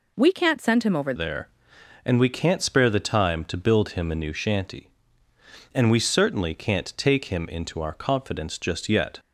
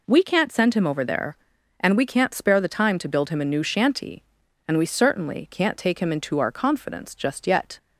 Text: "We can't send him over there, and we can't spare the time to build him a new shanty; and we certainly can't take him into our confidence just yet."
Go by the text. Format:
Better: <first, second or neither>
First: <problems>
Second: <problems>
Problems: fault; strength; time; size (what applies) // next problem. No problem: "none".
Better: second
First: changes voice at "there"; from 1.1 s on; 8.0 s long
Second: none